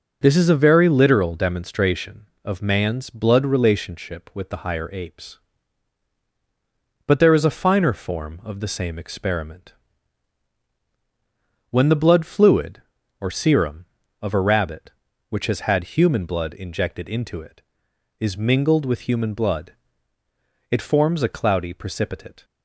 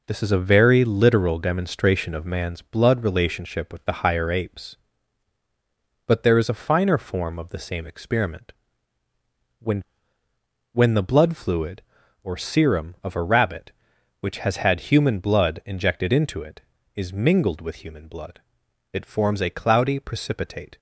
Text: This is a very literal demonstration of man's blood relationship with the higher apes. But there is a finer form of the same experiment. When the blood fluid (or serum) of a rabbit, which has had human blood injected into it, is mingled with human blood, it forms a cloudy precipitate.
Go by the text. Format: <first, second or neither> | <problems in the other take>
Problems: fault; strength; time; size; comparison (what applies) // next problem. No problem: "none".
first | says "When" twice; at 10.7 s